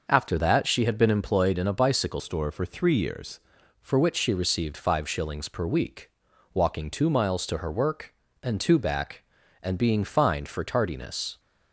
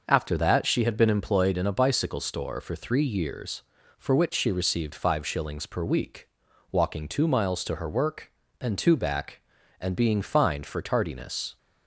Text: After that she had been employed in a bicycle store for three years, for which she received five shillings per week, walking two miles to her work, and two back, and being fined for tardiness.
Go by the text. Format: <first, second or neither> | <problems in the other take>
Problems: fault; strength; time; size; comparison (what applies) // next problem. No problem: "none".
second | changes voice from "store" to "years"; from 2.1 to 3.3 s; 1.2 s long